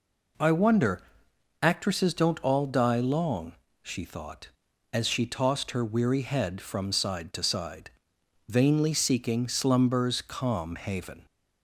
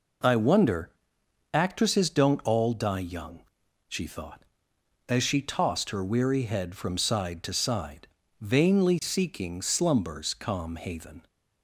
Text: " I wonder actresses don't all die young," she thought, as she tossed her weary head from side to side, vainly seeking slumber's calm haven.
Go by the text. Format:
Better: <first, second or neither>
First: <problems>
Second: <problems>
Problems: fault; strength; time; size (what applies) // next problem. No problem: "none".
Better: second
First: pauses between "wonder" and "actresses"; noticeable; at 1.0 s; 0.60 s long // says "long" for "young"; at 2.9 s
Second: pauses between "wonder" and "actresses"; noticeable; at 0.8 s; 0.64 s long